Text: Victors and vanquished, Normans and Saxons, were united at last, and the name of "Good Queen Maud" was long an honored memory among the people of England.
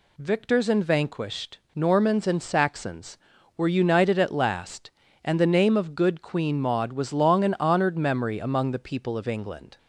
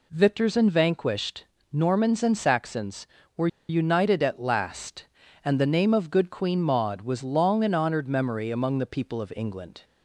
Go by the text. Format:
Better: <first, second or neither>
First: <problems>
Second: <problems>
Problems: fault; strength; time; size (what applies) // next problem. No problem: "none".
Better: first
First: none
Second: pauses between "were" and "united"; slight; at 3.4 s; 0.21 s long